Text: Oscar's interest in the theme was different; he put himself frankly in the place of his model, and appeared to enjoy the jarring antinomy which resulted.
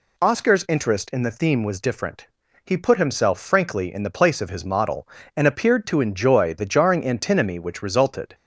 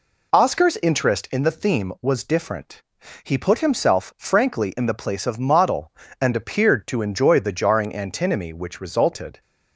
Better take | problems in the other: first | skips "his"; at 5.4 s

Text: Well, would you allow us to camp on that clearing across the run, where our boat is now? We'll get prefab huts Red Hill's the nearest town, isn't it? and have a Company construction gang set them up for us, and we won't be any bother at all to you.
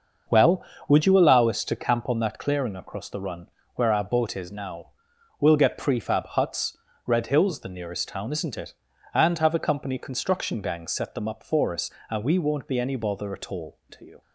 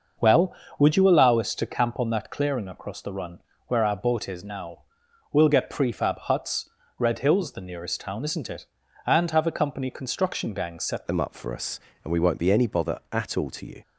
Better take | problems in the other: first | starts louder than the rest; noticeable; until 1.4 s; 6 dB; also in the first // pauses between "huts" and "Red"; slight; at 6.6 s; 0.30 s long; slight in the first // changes voice at "them"; from 11.0 s on; 2.8 s long

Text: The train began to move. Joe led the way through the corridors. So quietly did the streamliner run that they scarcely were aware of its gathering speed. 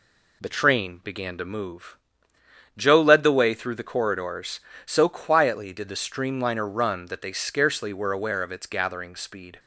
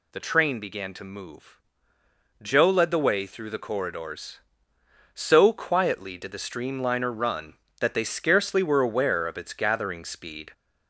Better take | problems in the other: first | gets louder; slight; throughout; 2.5 dB

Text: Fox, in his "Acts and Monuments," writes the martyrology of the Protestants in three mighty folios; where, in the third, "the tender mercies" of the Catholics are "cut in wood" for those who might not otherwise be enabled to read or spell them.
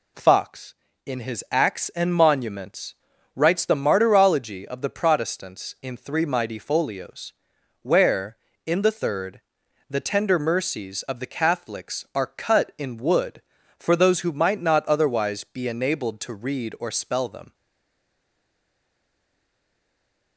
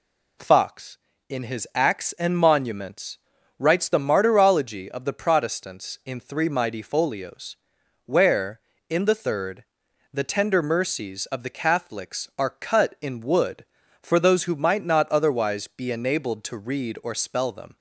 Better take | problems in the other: second | stays silent after the last word; strong; from 17.5 s on; 2.8 s long

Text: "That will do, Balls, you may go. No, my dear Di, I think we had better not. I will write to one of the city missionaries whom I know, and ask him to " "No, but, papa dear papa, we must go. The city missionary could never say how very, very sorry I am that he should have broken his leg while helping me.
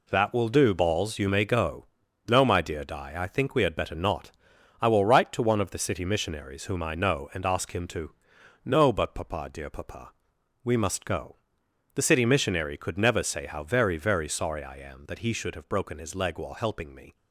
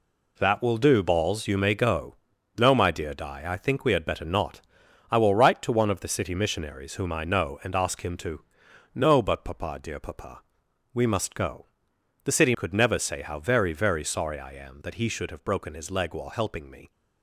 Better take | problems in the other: first | skips "missionary"; at 12.5 s

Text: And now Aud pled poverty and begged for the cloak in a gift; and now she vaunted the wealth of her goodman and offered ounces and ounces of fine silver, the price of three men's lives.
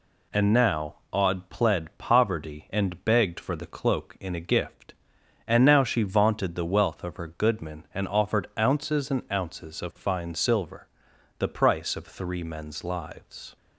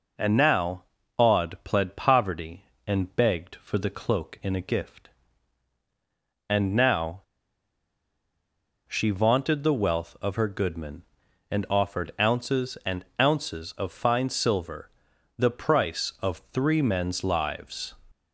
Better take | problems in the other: first | pauses between "now" and "Aud"; slight; at 0.8 s; 0.34 s long // pauses between "now" and "she"; strong; at 7.2 s; 1.6 s long // pauses between "and" and "ounces"; slight; at 13.0 s; 0.16 s long

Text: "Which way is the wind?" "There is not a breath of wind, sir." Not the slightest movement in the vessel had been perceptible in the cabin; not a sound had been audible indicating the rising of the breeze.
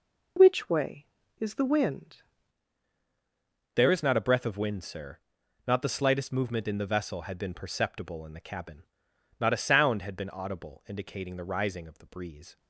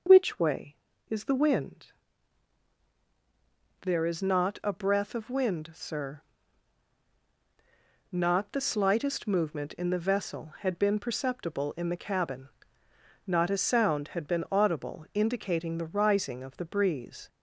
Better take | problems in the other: second | changes voice at "There"; from 3.7 s on; 8.8 s long

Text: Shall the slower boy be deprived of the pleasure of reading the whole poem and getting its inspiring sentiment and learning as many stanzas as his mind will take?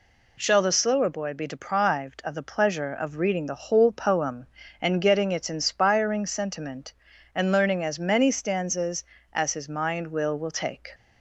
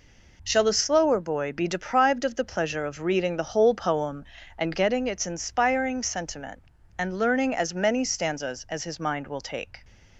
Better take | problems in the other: second | says "will" twice; at 10.3 s

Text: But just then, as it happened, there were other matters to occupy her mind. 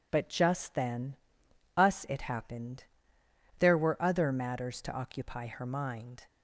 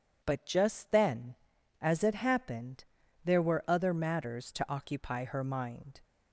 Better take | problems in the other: second | says "us" for "as"; at 1.7 s

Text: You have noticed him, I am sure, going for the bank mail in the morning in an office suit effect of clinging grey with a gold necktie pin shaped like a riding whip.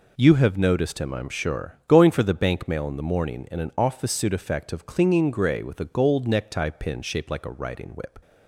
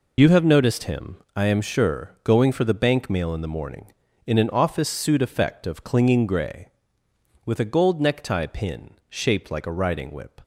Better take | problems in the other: first | loses the start of "You"; at 0.1 s; 60 ms // pauses between "pin" and "shaped"; slight; at 8.9 s; 0.18 s long

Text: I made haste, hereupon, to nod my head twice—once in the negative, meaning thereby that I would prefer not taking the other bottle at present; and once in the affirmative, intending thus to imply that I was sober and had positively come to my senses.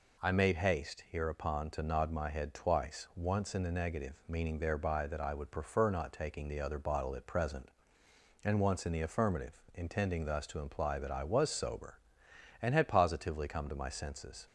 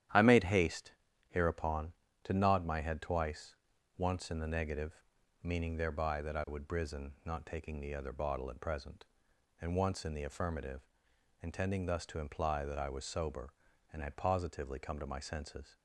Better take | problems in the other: first | starts louder than the rest; strong; until 1.4 s; 11 dB // says "brisen" for "prefer"; at 6.6 s

